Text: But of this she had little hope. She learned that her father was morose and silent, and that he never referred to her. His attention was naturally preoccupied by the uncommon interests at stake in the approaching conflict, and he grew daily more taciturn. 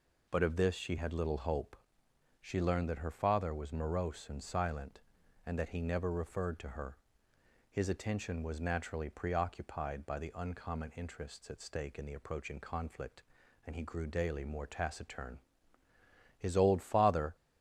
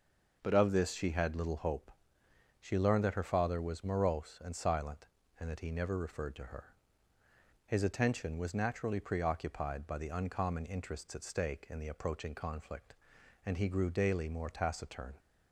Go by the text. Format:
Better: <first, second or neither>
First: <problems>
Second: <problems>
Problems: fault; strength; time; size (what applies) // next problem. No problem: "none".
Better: second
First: goes on to say "His old father"; noticeable; from 16.3 s on; 0.98 s long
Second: none